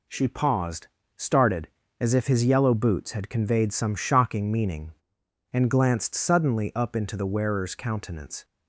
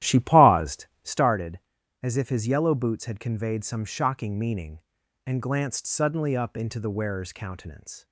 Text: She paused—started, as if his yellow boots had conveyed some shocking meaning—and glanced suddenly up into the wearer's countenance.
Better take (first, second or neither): first